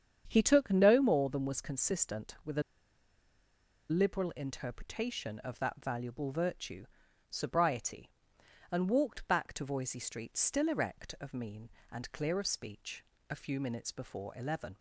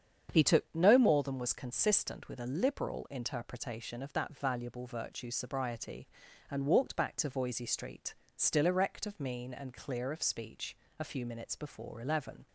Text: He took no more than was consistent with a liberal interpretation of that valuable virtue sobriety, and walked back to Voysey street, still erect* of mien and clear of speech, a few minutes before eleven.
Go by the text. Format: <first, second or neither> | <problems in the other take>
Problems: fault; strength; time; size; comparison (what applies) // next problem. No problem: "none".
second | starts louder than the rest; strong; until 1.2 s; 8 dB; strong in the second // pauses between "a" and "liberal"; strong; at 2.6 s; 1.2 s long // pauses between "virtue" and "sobriety"; at 6.8 s; 0.44 s long